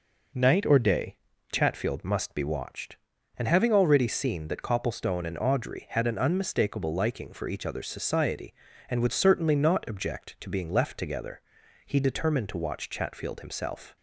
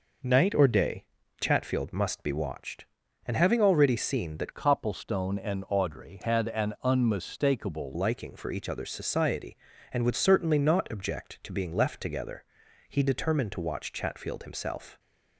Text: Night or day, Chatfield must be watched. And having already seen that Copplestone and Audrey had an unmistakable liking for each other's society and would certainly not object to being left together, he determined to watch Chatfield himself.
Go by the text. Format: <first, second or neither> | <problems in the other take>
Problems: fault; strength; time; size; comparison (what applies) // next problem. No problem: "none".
first | changes voice from "Copplestone" to "unmistakable"; from 4.5 to 7.9 s; 3.4 s long